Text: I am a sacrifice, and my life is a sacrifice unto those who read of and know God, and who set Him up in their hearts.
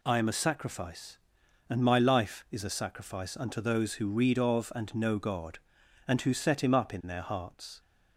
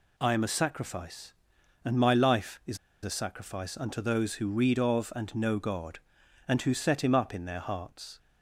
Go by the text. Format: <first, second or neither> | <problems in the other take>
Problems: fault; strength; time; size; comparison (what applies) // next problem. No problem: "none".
first | pauses between "is" and "a"; slight; at 2.7 s; 0.26 s long